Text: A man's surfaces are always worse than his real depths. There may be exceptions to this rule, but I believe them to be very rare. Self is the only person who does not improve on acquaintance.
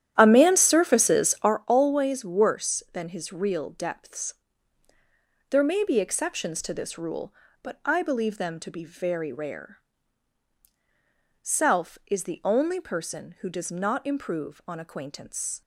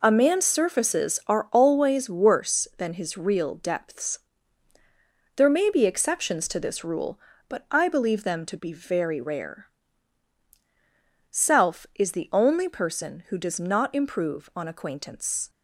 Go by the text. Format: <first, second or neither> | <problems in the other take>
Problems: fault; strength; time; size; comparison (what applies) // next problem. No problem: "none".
second | starts louder than the rest; strong; until 1.6 s; 11 dB